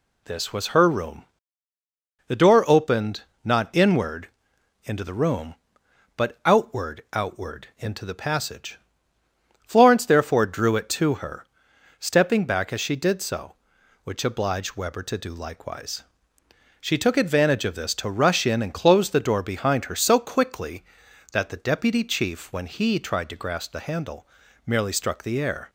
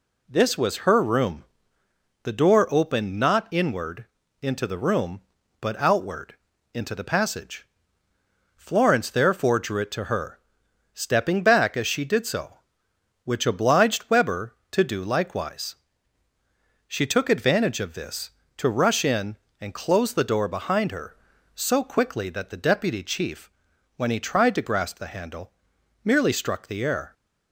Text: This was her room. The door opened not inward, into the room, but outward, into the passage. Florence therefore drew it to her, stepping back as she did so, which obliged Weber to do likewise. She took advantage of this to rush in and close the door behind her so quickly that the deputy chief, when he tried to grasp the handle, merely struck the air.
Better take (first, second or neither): second